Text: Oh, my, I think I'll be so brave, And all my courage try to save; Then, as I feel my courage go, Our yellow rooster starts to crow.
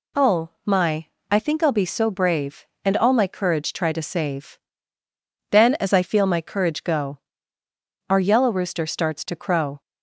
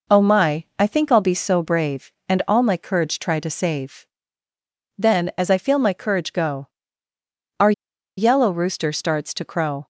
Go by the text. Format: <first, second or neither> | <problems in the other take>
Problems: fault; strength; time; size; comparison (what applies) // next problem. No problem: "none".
first | pauses between "Our" and "yellow"; noticeable; at 7.7 s; 0.46 s long